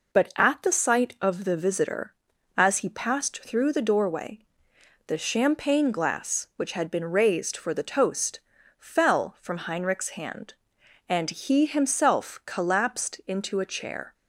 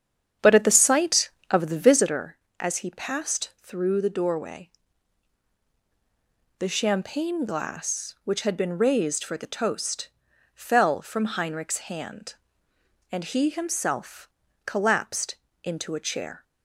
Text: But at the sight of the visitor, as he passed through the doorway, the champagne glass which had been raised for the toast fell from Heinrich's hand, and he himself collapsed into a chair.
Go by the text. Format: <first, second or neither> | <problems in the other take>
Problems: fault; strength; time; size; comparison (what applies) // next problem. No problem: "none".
first | starts louder than the rest; strong; until 2.1 s; 8.5 dB // pauses between "toast" and "fell"; noticeable; at 10.0 s; 0.48 s long; also in the first // pauses between "himself" and "collapsed"; at 14.2 s; 0.38 s long // pauses between "collapsed" and "into"; slight; at 15.3 s; 0.28 s long